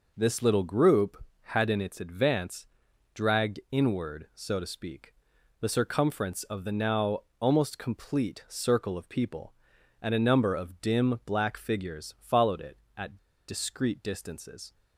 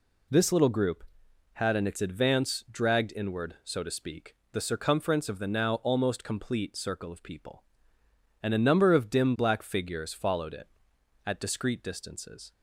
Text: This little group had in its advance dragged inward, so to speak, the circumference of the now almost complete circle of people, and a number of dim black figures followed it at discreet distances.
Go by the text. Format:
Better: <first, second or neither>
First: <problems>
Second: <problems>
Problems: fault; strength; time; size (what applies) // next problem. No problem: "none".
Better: second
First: pauses between "advance" and "dragged"; noticeable; at 2.6 s; 0.48 s long // pauses between "now" and "almost"; slight; at 7.1 s; 0.20 s long // pauses between "at" and "discreet"; slight; at 13.1 s; 0.31 s long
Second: none